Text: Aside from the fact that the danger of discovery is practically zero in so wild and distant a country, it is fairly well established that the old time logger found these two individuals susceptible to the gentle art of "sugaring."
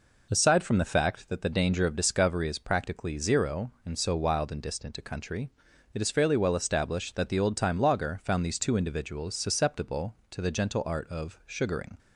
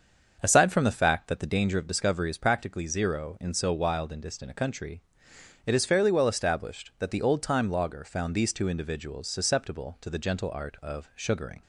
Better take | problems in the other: first | starts louder than the rest; until 1.7 s; 6.5 dB

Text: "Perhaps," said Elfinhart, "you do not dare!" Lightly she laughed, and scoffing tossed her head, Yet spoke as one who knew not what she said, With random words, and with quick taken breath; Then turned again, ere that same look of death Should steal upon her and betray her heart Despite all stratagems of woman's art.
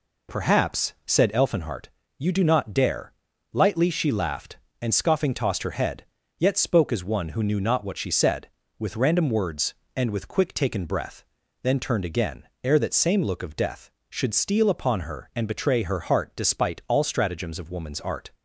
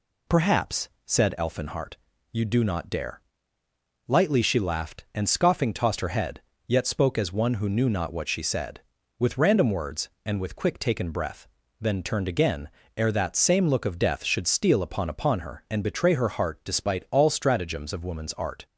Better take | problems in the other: first | says "upon" twice; at 15.0 s

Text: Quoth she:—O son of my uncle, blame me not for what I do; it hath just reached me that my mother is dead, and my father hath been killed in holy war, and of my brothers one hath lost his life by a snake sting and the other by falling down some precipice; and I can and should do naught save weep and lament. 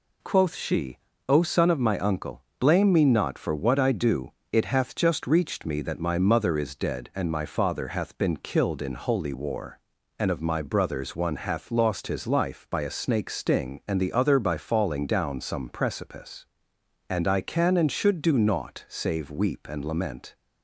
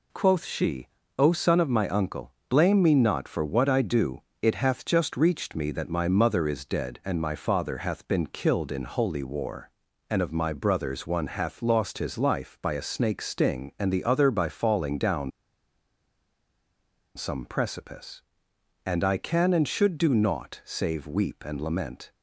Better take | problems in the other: first | pauses between "down" and "some"; strong; at 15.3 s; 1.8 s long

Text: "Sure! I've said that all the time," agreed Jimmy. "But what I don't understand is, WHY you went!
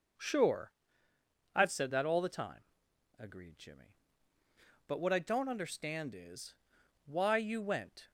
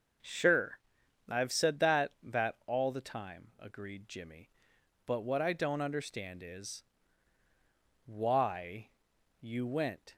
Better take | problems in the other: first | starts louder than the rest; until 1.6 s; 6 dB // says "that" twice; at 2.2 s // pauses between "WHY" and "you"; noticeable; at 8.8 s; 0.50 s long

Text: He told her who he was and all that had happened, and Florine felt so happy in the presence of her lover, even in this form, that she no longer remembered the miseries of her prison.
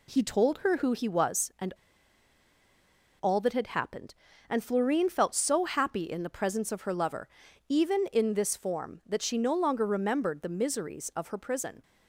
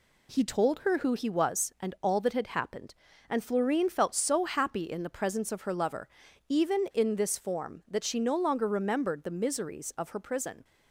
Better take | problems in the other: second | pauses between "and" and "all"; strong; at 1.7 s; 1.5 s long

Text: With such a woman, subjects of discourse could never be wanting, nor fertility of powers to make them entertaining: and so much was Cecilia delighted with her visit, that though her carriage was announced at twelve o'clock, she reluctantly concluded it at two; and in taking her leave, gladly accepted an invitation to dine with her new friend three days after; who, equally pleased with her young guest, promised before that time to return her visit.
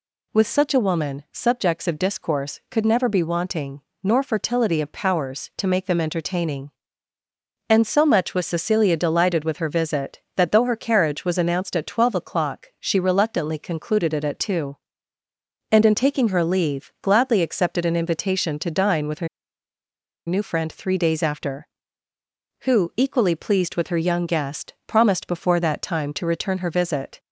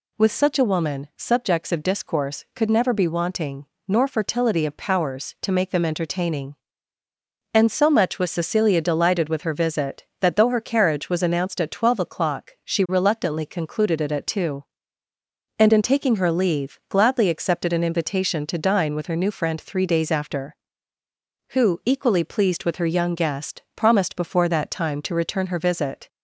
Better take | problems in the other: second | pauses between "her" and "new"; at 19.2 s; 1.0 s long

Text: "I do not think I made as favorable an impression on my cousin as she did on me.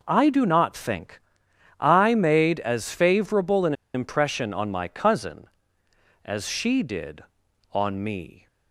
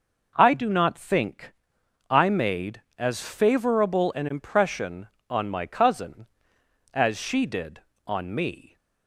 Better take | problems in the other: second | pauses between "think" and "I"; noticeable; at 1.1 s; 0.60 s long; noticeable in the second // pauses between "an" and "impression"; slight; at 3.7 s; 0.20 s long

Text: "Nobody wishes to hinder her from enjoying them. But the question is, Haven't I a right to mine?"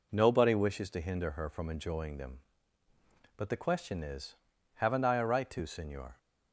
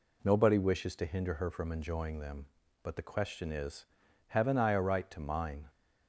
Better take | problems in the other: second | says "senor" for "mine"; at 5.6 s

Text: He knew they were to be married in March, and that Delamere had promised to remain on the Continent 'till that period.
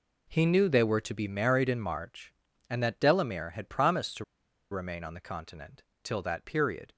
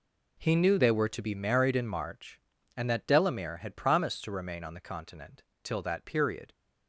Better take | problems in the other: second | pauses between "to" and "remain"; noticeable; at 4.2 s; 0.47 s long // pauses between "Continent" and "till"; slight; at 5.8 s; 0.20 s long; slight in the second

